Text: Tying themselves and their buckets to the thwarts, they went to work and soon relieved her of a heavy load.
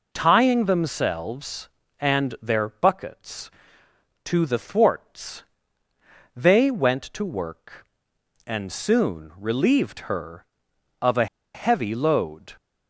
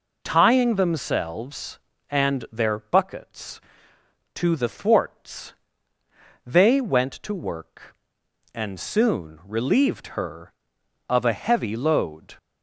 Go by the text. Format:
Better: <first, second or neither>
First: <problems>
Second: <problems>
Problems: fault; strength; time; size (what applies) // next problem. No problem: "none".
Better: second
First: pauses between "a" and "heavy"; slight; at 11.2 s; 0.28 s long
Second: none